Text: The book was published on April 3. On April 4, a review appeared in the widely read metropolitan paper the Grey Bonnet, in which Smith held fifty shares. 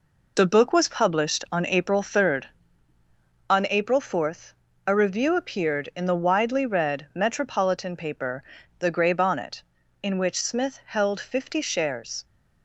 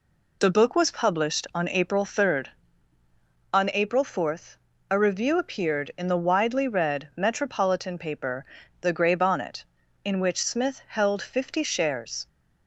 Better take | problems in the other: second | gets quieter; throughout; 7 dB // pauses between "paper" and "the"; slight; at 8.4 s; 0.34 s long; slight in the second

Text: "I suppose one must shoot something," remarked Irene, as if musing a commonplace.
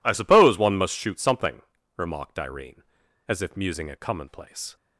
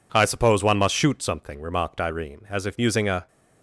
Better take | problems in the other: first | stops before "commonplace"; at 3.2 s

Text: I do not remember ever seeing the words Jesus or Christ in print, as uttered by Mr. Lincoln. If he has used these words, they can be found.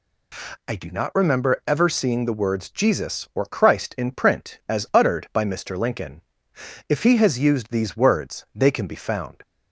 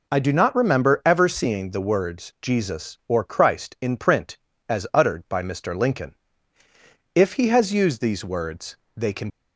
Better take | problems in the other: first | stops before "be found"; at 9.3 s

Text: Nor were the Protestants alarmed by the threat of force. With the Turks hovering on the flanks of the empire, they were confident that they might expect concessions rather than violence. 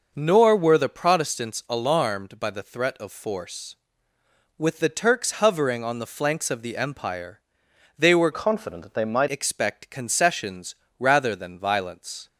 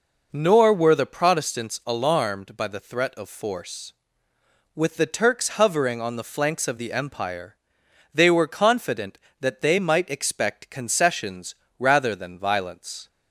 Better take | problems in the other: second | changes voice from "confident" to "might"; from 8.3 to 9.2 s; 0.9 s long // pauses between "concessions" and "rather"; slight; at 10.7 s; 0.24 s long; slight in the second

